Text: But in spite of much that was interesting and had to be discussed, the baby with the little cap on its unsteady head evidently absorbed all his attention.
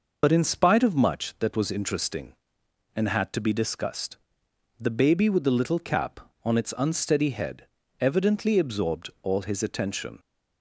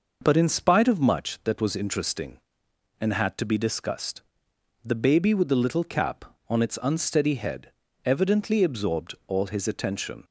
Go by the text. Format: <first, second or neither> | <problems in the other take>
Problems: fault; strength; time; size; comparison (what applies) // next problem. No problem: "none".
second | loses the start of "But"; at 0.2 s; 65 ms // pauses between "head" and "evidently"; slight; at 7.6 s; 0.32 s long; slight in the second